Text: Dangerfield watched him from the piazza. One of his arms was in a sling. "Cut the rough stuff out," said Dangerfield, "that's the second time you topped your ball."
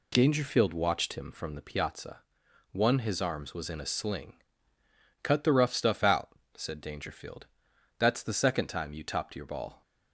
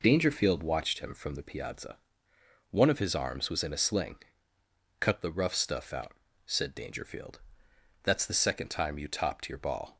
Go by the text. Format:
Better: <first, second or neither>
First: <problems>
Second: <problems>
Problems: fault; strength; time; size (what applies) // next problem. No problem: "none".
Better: second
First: skips "of"; at 2.9 s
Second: none